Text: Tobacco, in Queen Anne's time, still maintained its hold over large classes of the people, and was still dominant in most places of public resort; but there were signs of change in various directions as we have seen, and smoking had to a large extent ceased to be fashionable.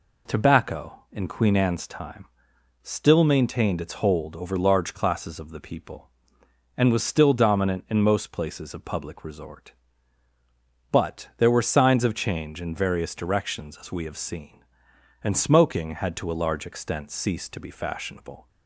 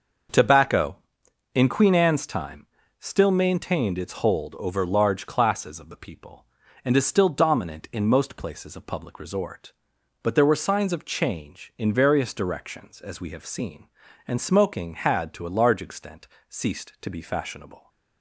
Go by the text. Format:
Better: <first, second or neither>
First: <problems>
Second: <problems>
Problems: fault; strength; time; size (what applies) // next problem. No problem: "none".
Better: first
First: none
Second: starts louder than the rest; until 1.9 s; 6.5 dB // says "is" for "was"; at 6.9 s // pauses between "extent" and "ceased"; slight; at 16.2 s; 0.20 s long